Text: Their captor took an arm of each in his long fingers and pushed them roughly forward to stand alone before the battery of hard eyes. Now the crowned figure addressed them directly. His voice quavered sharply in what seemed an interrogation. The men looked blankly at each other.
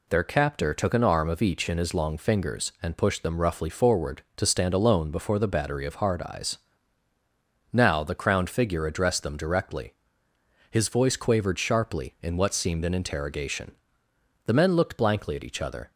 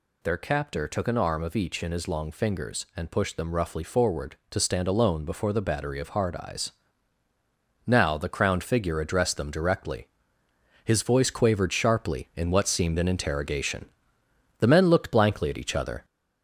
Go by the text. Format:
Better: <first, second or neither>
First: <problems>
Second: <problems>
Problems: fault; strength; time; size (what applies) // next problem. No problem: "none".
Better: first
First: none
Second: gets louder; throughout; 3.5 dB